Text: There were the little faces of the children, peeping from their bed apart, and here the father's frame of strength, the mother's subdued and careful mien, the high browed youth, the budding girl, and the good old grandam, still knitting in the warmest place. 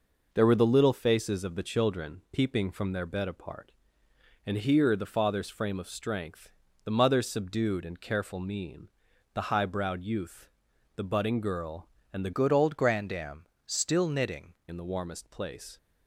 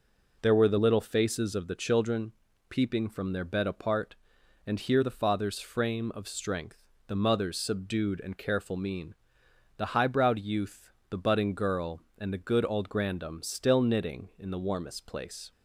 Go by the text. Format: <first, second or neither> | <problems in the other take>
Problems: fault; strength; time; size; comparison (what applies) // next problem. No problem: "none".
second | changes voice from "good" to "knitting"; from 12.3 to 14.5 s; 2.2 s long